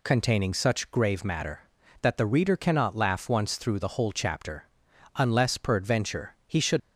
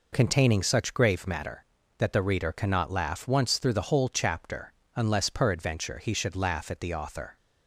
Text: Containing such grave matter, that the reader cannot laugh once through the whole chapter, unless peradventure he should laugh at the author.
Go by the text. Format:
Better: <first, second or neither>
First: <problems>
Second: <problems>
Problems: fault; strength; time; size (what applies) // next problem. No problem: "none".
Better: second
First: stops before "laugh at the author"; at 6.8 s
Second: none